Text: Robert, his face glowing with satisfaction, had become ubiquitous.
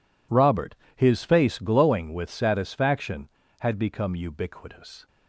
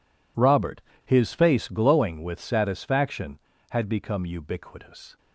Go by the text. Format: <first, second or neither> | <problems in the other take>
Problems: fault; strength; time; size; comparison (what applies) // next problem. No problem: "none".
neither | none